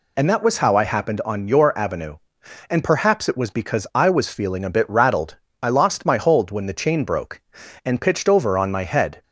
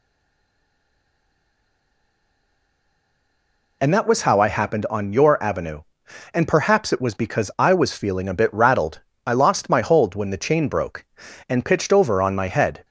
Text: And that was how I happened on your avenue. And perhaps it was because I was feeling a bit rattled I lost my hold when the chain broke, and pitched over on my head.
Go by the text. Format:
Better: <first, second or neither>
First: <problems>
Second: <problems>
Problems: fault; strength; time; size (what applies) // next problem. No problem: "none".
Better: first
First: pauses between "rattled" and "I"; slight; at 5.3 s; 0.26 s long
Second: stays silent before the first word; strong; until 3.8 s; 3.8 s long // pauses between "rattled" and "I"; slight; at 8.9 s; 0.26 s long